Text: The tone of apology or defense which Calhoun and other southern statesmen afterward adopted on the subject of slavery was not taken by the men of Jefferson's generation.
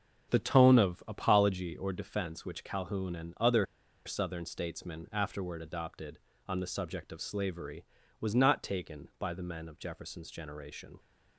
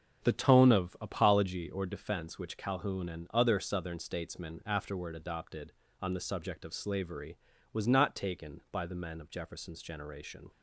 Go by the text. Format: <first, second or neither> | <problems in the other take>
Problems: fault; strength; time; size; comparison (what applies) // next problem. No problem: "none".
second | starts louder than the rest; strong; until 1.3 s; 7.5 dB; strong in the second // pauses between "other" and "southern"; at 3.6 s; 0.40 s long